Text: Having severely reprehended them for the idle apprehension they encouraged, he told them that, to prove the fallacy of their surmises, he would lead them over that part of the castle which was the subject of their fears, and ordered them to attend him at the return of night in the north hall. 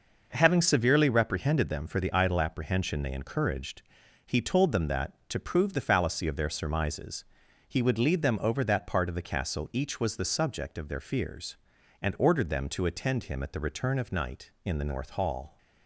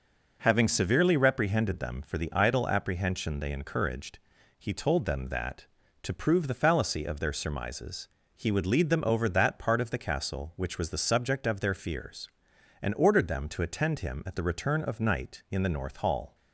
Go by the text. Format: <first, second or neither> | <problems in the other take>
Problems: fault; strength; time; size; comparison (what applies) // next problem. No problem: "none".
second | says "each" for "which"; at 9.7 s